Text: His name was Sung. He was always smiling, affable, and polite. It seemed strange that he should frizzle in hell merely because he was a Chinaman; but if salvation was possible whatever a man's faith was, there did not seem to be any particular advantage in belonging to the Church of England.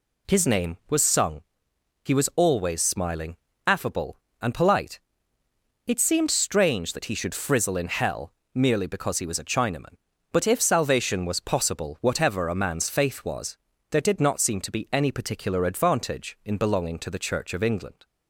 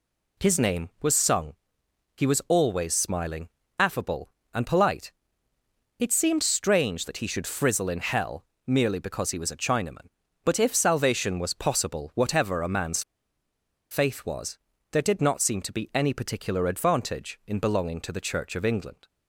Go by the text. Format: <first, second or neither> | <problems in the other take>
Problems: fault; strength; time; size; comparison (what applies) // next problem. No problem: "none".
first | pauses between "hell" and "merely"; slight; at 8.4 s; 0.26 s long; slight in the first // pauses between "man's" and "faith"; noticeable; at 13.0 s; 0.89 s long